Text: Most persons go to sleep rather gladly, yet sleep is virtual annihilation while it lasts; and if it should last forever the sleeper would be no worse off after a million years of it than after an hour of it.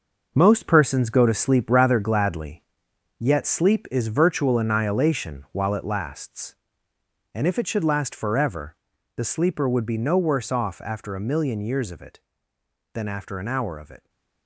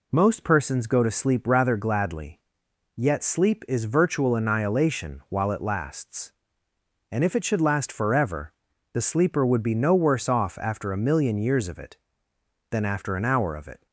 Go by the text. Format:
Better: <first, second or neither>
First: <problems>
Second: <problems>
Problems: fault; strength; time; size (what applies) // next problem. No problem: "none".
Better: second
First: gets quieter; strong; throughout; 8 dB // pauses between "forever" and "the"; at 8.7 s; 0.40 s long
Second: pauses between "forever" and "the"; at 8.5 s; 0.40 s long